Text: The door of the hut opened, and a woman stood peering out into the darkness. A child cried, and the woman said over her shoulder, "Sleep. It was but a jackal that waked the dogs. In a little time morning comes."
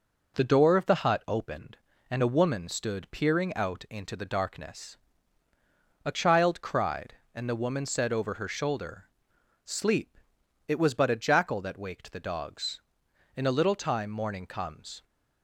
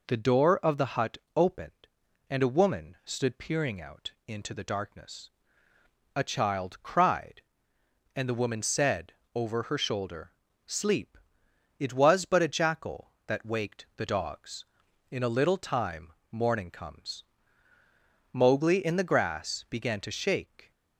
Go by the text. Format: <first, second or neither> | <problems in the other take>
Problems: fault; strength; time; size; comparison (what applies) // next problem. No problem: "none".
first | pauses between "hut" and "opened"; slight; at 1.1 s; 0.18 s long // pauses between "out" and "into"; slight; at 4.1 s; 0.16 s long // pauses between "said" and "over"; slight; at 9.1 s; 0.20 s long // pauses between "time" and "morning"; slight; at 16.1 s; 0.20 s long // goes on to say "Mowgli in the grass began to shake"; strong; from 18.3 s on; 2.3 s long